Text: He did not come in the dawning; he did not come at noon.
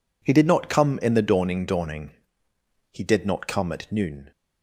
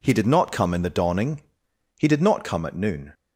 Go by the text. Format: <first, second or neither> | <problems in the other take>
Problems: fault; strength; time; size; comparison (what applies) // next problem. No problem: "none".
second | says "dawning" twice; at 1.6 s